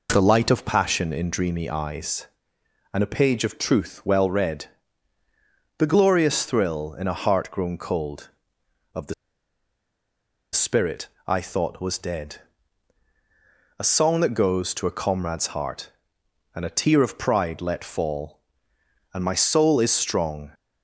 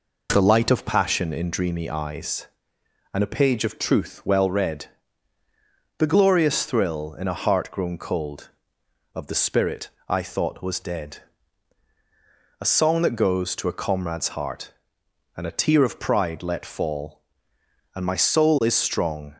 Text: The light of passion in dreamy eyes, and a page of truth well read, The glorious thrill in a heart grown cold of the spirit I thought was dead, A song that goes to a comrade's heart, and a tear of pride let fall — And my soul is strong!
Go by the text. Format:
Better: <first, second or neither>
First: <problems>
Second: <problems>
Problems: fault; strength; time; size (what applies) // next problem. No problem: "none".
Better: second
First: pauses between "the" and "spirit"; strong; at 9.1 s; 1.3 s long // pauses between "spirit" and "I"; slight; at 11.0 s; 0.18 s long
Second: pauses between "spirit" and "I"; slight; at 9.8 s; 0.18 s long